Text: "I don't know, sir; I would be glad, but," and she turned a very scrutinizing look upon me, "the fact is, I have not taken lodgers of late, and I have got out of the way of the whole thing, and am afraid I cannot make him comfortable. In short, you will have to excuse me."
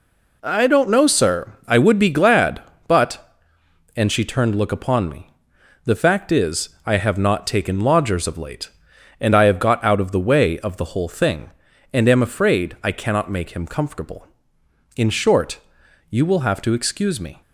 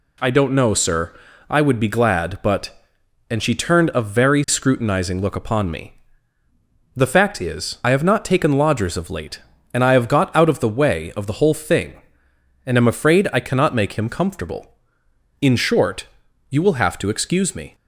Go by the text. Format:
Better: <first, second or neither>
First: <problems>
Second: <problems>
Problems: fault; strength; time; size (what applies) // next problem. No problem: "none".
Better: second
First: skips "a very scrutinizing"; at 4.5 s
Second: none